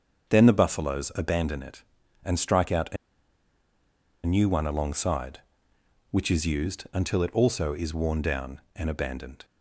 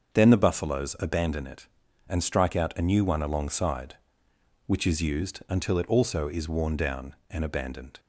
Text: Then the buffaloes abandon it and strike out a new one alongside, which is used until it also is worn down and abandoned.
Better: second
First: starts louder than the rest; until 1.3 s; 6.5 dB // pauses between "a" and "new"; strong; at 2.9 s; 1.2 s long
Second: starts louder than the rest; until 1.1 s; 6.5 dB

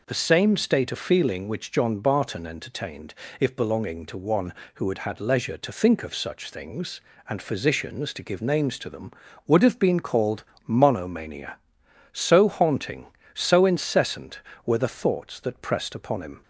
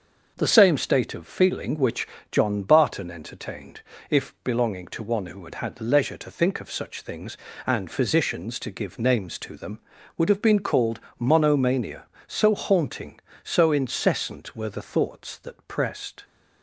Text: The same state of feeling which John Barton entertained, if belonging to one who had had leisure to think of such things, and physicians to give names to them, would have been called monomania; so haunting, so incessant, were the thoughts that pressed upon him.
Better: first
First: pauses between "called" and "monomania"; slight; at 10.4 s; 0.22 s long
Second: starts louder than the rest; noticeable; until 1.3 s; 6 dB // pauses between "which" and "John"; slight; at 2.0 s; 0.24 s long // pauses between "called" and "monomania"; slight; at 10.9 s; 0.20 s long // stops before "upon him"; at 16.2 s

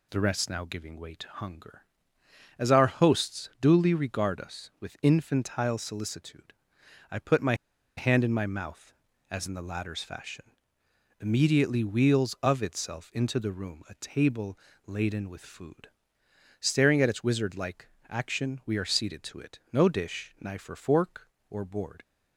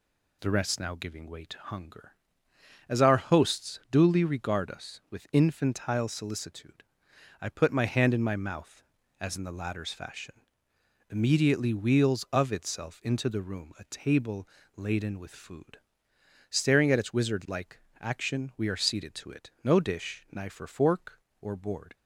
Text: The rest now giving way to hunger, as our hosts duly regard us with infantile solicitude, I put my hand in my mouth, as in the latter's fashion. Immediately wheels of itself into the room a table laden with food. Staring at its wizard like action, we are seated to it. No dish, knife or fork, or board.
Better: second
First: pauses between "my" and "hand"; at 7.5 s; 0.43 s long // pauses between "table" and "laden"; slight; at 14.5 s; 0.30 s long // pauses between "like" and "action"; slight; at 17.8 s; 0.20 s long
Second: pauses between "table" and "laden"; slight; at 14.4 s; 0.30 s long // pauses between "like" and "action"; slight; at 17.7 s; 0.20 s long

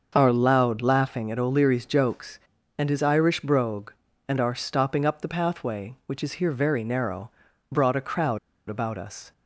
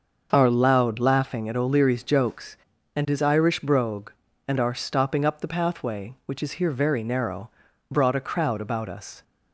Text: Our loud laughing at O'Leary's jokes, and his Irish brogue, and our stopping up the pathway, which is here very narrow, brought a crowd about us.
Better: second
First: starts louder than the rest; until 1.1 s; 6.5 dB // pauses between "crowd" and "about"; slight; at 8.3 s; 0.29 s long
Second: starts louder than the rest; until 1.3 s; 6.5 dB

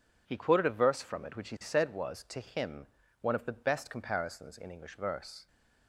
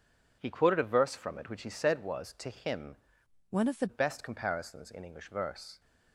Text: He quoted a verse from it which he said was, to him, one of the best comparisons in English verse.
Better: first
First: none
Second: changes voice from "one" to "the"; from 3.5 to 3.8 s; 0.3 s long

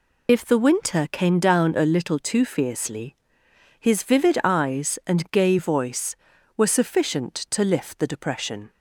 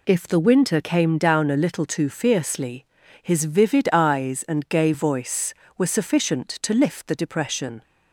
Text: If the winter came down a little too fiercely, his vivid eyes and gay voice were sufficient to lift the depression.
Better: second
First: loses the start of "If"; at 0.2 s; 25 ms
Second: none

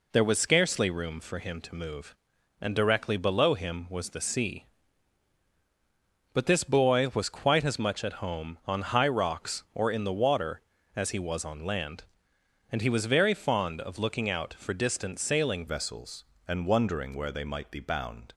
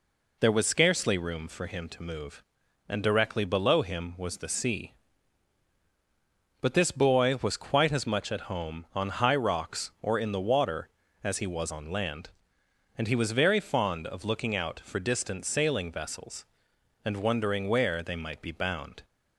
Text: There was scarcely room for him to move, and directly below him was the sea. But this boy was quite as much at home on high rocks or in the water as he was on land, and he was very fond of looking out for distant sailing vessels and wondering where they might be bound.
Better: second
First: changes voice at "vessels"; from 15.6 s on; 2.7 s long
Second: none

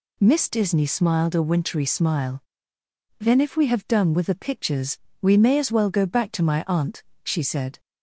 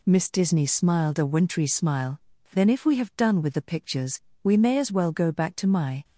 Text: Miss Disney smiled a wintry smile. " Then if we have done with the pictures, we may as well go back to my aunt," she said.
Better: first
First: none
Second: stops before "aunt she said"; at 6.0 s

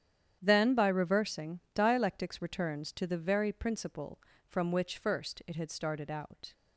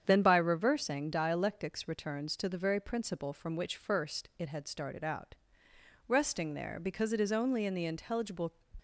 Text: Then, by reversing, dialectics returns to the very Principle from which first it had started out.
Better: first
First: starts louder than the rest; strong; until 1.4 s; 9.5 dB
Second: starts louder than the rest; strong; until 1.0 s; 8 dB // goes on to say "Resting there because it is only in the intelligible"; strong; from 6.0 s on; 2.4 s long

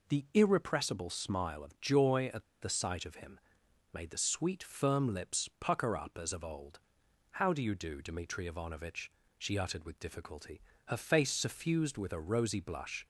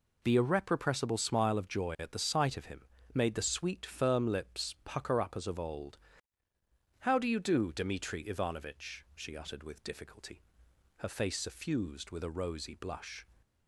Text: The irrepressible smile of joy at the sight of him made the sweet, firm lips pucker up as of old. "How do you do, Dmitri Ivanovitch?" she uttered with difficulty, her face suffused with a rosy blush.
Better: second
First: pauses between "at" and "the"; slight; at 2.4 s; 0.18 s long // pauses between "him" and "made"; noticeable; at 3.3 s; 0.54 s long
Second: pauses between "him" and "made"; slight; at 2.8 s; 0.30 s long

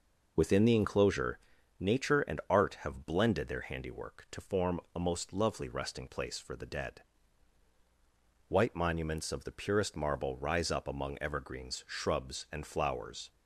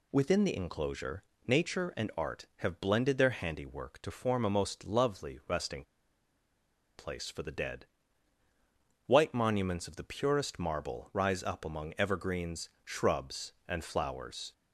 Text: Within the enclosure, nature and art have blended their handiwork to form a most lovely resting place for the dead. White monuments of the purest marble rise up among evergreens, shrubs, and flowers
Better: first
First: none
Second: pauses between "resting" and "place"; at 5.8 s; 1.1 s long

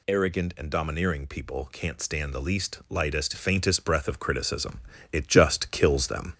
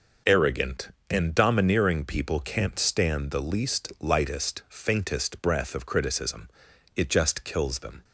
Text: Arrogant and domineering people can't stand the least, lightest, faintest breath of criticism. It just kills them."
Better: second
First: gets louder; slight; throughout; 2.5 dB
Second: none

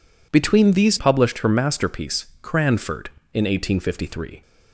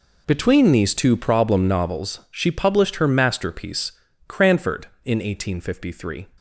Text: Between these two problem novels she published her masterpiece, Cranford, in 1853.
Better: second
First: skips "two problem novels she"; at 0.9 s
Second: none

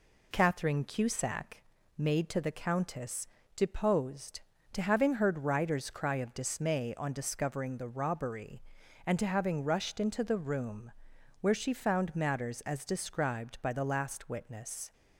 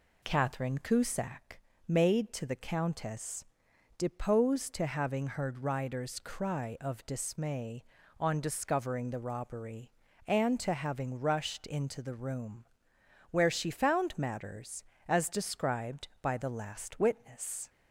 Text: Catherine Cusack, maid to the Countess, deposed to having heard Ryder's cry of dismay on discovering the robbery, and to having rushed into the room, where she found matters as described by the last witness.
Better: neither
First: none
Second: none

